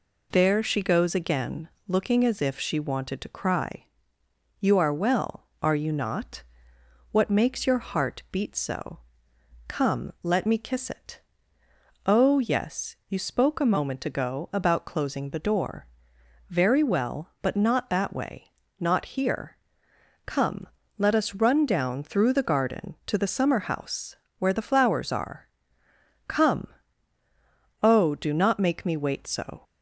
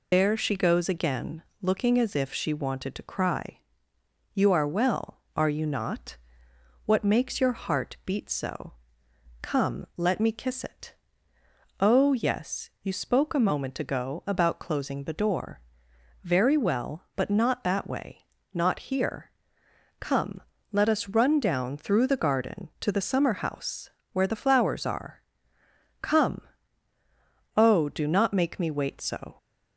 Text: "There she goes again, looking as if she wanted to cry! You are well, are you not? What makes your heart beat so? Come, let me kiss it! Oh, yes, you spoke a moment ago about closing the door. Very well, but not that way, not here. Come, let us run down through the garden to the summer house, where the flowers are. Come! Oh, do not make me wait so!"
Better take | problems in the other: first | loses the start of "There"; at 0.1 s; 80 ms

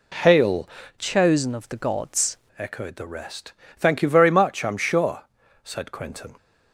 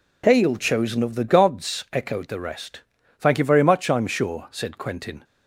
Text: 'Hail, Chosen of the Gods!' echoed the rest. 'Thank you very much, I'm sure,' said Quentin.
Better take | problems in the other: second | changes voice from "Chosen" to "Gods"; from 0.9 to 2.3 s; 1.4 s long

